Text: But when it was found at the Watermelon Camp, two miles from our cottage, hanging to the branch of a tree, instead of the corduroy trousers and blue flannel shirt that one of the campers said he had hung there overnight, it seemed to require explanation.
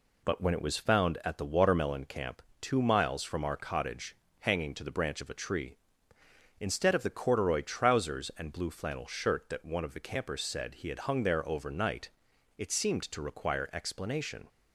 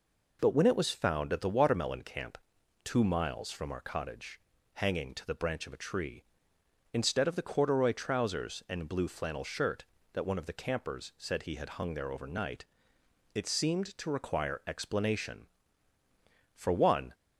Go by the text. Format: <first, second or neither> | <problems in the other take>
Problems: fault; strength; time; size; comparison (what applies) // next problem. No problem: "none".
first | goes on to say "For one"; from 16.5 s on; 0.58 s long